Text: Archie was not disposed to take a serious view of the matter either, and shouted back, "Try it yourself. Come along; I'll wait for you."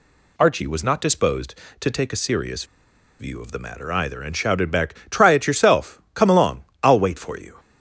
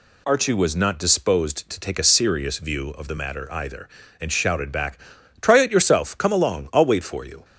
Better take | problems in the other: second | pauses between "serious" and "view"; noticeable; at 2.6 s; 0.55 s long

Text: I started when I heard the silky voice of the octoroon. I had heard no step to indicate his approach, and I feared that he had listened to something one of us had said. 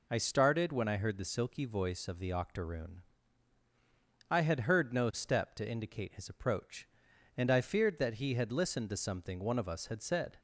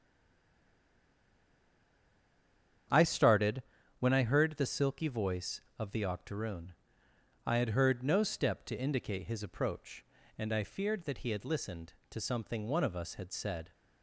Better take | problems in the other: first | stays silent before the first word; strong; until 2.8 s; 2.8 s long // starts louder than the rest; strong; until 4.2 s; 8.5 dB // pauses between "started" and "when"; at 3.6 s; 0.38 s long

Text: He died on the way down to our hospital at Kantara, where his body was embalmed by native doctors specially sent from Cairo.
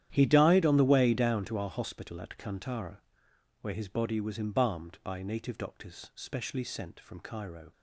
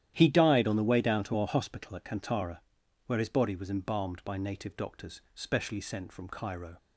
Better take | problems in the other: second | gets quieter; strong; throughout; 16 dB // starts louder than the rest; strong; until 1.1 s; 11 dB; strong in the second

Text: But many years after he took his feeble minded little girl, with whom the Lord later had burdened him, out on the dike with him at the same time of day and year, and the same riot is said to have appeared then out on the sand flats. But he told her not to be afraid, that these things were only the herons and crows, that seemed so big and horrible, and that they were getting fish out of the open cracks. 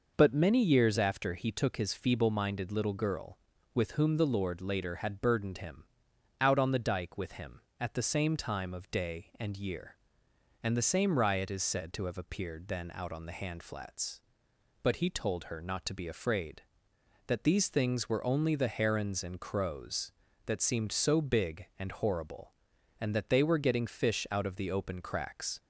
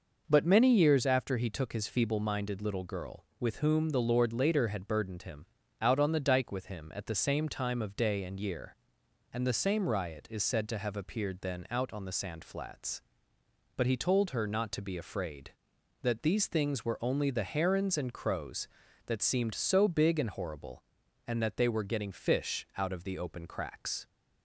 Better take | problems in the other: second | says "hand" for "sand"; at 13.3 s

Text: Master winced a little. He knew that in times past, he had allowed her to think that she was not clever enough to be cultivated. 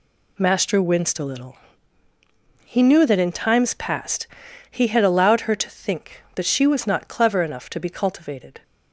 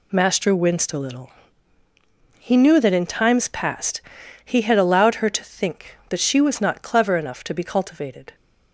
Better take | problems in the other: neither | none

